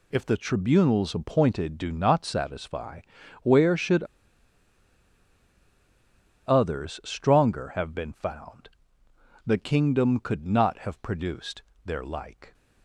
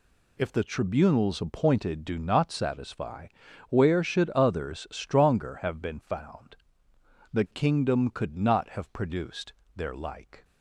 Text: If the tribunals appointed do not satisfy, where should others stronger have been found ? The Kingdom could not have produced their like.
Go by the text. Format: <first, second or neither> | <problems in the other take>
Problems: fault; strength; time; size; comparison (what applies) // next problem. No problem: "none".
second | pauses between "should" and "others"; strong; at 4.0 s; 2.4 s long // pauses between "produced" and "their"; slight; at 11.6 s; 0.24 s long; slight in the second